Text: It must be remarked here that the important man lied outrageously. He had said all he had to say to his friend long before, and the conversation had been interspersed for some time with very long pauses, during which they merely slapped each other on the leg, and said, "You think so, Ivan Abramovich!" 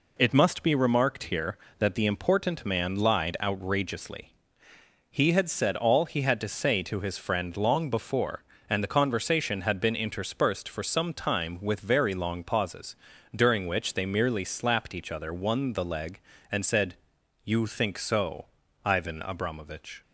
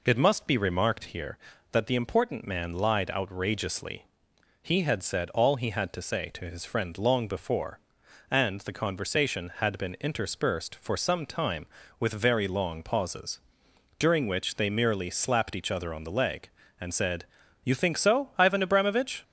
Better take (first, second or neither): second